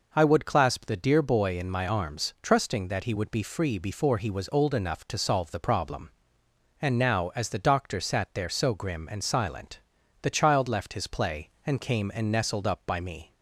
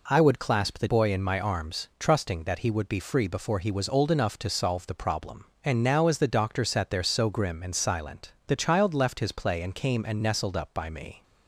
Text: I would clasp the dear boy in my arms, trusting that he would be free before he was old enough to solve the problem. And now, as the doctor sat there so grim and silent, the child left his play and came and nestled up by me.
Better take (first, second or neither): first